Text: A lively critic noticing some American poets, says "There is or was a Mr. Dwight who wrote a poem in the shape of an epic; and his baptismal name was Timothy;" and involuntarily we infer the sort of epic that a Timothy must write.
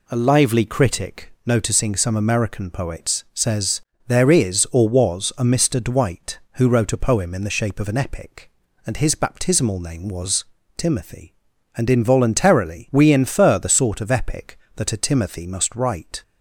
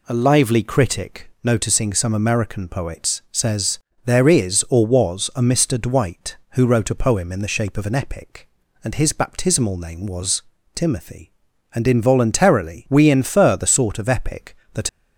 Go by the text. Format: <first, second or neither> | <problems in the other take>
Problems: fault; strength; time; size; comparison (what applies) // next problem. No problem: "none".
first | pauses between "says" and "There"; slight; at 3.7 s; 0.26 s long; slight in the first // pauses between "was" and "Timothy"; slight; at 10.4 s; 0.32 s long; slight in the first // stops before "a Timothy must write"; at 14.8 s